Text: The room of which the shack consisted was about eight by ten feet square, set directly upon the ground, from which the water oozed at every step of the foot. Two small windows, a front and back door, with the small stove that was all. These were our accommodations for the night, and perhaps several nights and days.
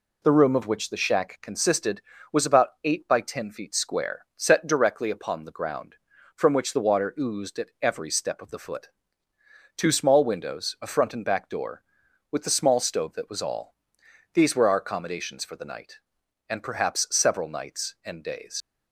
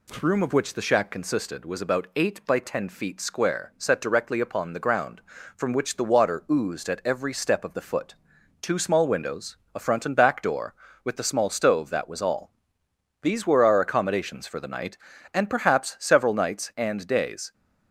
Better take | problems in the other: second | pauses between "about" and "eight"; slight; at 2.6 s; 0.16 s long // leaves "days" unfinished; at 18.6 s; 85 ms

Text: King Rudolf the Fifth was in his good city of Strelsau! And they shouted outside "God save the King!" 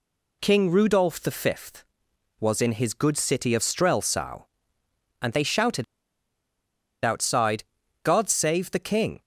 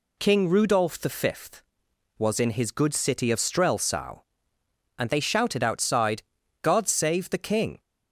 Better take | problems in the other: second | pauses between "shouted" and "outside"; at 5.8 s; 1.2 s long // pauses between "outside" and "God"; at 7.6 s; 0.40 s long; also in the second

